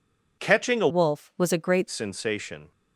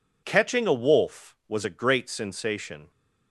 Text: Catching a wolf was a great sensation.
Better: second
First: changes voice from "wolf" to "great"; from 0.8 to 1.8 s; 1.0 s long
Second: none

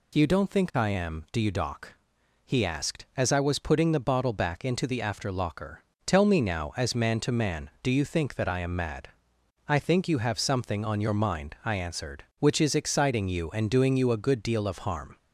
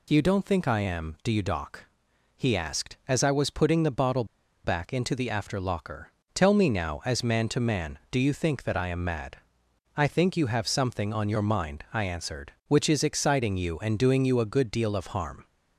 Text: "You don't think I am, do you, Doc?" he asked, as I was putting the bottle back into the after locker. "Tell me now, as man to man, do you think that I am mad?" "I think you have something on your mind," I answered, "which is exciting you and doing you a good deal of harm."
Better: first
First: none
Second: pauses between "bottle" and "back"; at 4.2 s; 0.39 s long

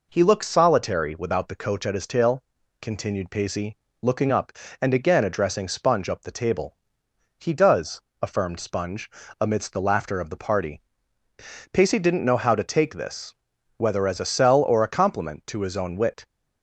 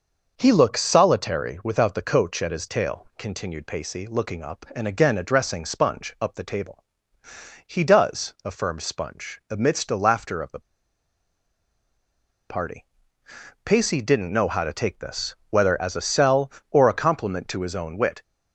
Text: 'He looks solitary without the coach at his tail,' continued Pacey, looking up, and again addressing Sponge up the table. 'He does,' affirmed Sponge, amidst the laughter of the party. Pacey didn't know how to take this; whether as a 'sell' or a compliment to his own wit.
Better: first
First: none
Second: pauses between "the" and "party"; strong; at 10.5 s; 1.8 s long

